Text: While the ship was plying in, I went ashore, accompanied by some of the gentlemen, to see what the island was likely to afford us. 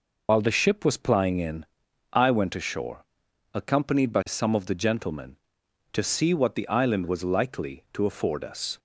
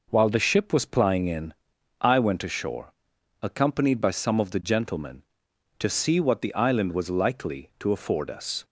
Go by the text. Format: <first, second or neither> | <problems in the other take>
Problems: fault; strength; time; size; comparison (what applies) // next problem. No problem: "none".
second | loses the start of "While"; at 0.2 s; 85 ms